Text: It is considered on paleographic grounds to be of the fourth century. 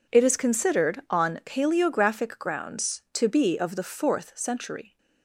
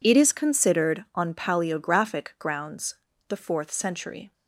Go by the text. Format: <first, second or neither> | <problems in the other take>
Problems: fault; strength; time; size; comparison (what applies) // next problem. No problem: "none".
first | skips "to be of"; at 3.1 s